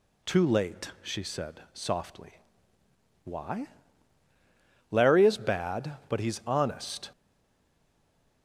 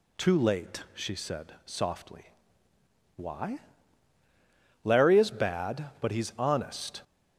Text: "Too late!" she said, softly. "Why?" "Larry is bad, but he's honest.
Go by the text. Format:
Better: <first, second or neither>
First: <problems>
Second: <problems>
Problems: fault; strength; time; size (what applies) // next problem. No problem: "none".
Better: second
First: stays silent after the last word; noticeable; from 7.1 s on; 1.3 s long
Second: none